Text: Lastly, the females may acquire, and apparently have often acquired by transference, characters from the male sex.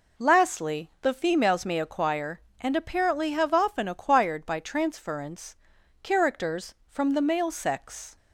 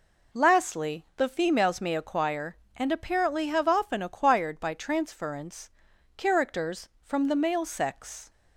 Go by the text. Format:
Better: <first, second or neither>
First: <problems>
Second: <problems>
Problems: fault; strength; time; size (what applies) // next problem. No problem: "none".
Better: neither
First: none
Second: none